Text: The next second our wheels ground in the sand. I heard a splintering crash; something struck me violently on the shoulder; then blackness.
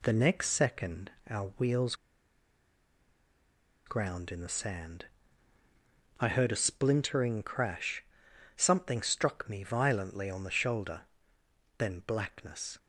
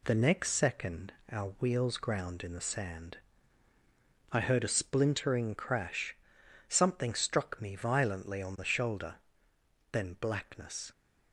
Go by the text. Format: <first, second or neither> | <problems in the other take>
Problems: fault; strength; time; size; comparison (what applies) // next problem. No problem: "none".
second | pauses between "second" and "our"; slight; at 1.1 s; 0.18 s long; slight in the second // pauses between "wheels" and "ground"; strong; at 1.9 s; 1.9 s long